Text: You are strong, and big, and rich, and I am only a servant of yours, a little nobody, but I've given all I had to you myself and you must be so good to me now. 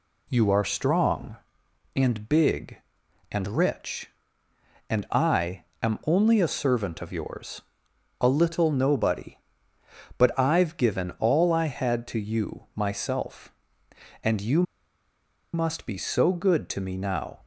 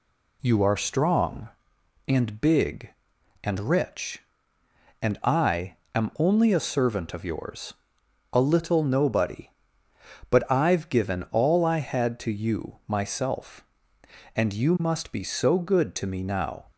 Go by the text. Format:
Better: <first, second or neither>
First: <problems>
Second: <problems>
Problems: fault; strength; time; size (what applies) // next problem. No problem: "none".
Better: second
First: pauses between "I" and "am"; slight; at 5.6 s; 0.18 s long // pauses between "you" and "must"; noticeable; at 14.6 s; 0.91 s long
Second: pauses between "I" and "am"; slight; at 5.7 s; 0.18 s long